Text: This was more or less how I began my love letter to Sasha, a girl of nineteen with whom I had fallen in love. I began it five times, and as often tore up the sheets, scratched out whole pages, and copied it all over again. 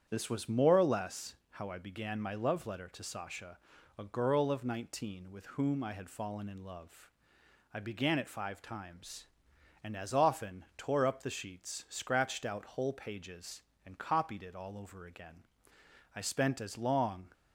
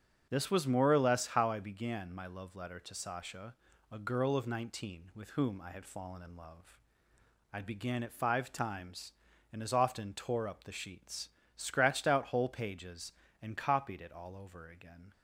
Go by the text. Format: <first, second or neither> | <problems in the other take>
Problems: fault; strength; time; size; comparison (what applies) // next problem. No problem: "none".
second | starts louder than the rest; strong; until 1.1 s; 8.5 dB; also in the second // pauses between "less" and "how"; slight; at 1.3 s; 0.16 s long // goes on to say "I spent as long"; noticeable; from 16.1 s on; 1.1 s long